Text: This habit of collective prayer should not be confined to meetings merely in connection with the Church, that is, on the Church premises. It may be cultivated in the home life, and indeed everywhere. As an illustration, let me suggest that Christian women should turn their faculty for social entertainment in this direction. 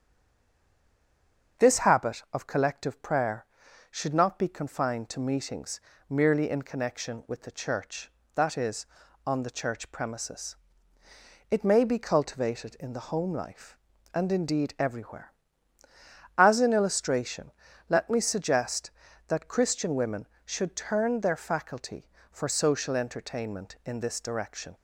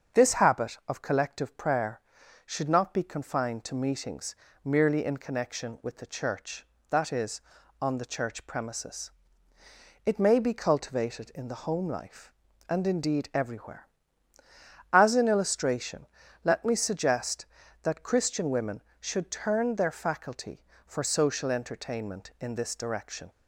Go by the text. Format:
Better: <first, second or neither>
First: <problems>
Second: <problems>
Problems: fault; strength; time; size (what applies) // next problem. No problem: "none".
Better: second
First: stays silent before the first word; noticeable; until 1.5 s; 1.5 s long // starts louder than the rest; strong; until 2.7 s; 7 dB // pauses between "meetings" and "merely"; slight; at 5.7 s; 0.30 s long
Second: starts louder than the rest; strong; until 1.2 s; 7 dB // pauses between "meetings" and "merely"; slight; at 4.3 s; 0.30 s long